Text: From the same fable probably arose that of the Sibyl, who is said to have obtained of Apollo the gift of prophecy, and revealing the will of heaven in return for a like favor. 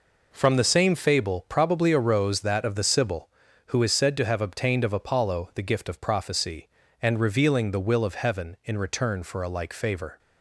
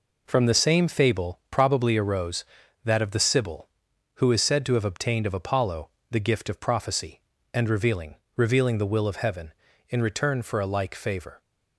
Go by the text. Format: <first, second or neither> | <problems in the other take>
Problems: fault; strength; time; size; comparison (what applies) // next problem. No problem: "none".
first | pauses between "Apollo" and "the"; slight; at 5.8 s; 0.22 s long // says "revealing" twice; at 8.3 s